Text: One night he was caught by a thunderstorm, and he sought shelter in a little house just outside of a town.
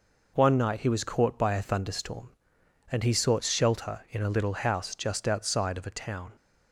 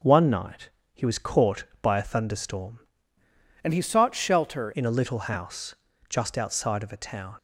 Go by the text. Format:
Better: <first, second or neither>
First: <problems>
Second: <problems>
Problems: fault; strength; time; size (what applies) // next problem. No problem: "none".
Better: first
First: none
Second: pauses between "night" and "he"; slight; at 0.7 s; 0.24 s long // changes voice from "and" to "shelter"; from 3.6 to 4.7 s; 1.1 s long // pauses between "house" and "just"; slight; at 5.7 s; 0.34 s long